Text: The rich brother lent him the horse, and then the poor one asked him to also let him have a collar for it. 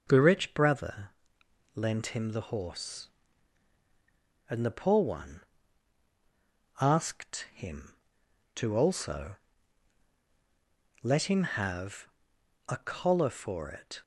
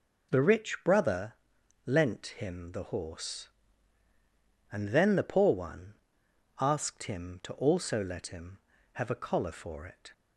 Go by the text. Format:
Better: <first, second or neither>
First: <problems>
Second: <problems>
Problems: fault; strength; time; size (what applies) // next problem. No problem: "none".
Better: second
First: pauses between "brother" and "lent"; noticeable; at 1.0 s; 0.66 s long // skips "then"; at 4.6 s // pauses between "one" and "asked"; strong; at 5.4 s; 1.3 s long // pauses between "also" and "let"; strong; at 9.3 s; 1.6 s long // pauses between "have" and "a"; noticeable; at 12.0 s; 0.62 s long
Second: pauses between "brother" and "lent"; noticeable; at 1.3 s; 0.54 s long // pauses between "one" and "asked"; noticeable; at 5.9 s; 0.66 s long